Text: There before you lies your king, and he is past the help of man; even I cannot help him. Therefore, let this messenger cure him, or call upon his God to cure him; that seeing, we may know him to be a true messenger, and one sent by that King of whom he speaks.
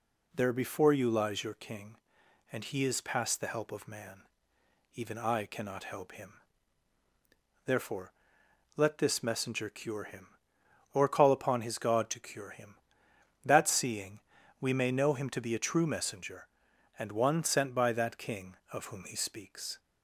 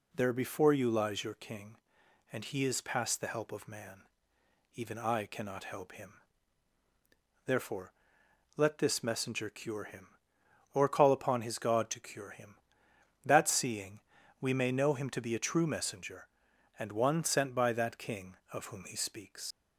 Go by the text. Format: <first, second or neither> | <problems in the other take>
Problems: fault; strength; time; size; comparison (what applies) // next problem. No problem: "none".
first | leaves "speaks" unfinished; at 19.5 s; 85 ms